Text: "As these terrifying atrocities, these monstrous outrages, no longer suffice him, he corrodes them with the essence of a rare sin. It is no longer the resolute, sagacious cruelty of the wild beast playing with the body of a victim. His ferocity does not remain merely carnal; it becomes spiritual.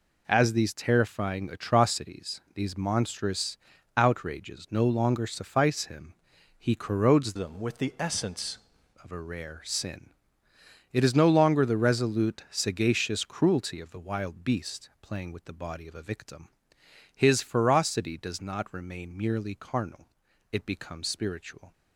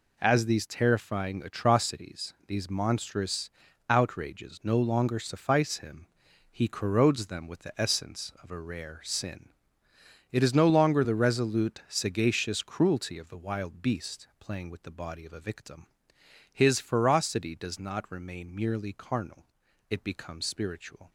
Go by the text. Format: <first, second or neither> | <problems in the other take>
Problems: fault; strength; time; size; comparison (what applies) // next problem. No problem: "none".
second | pauses between "monstrous" and "outrages"; at 3.5 s; 0.38 s long; also in the second // changes voice from "them" to "essence"; from 7.3 to 8.5 s; 1.2 s long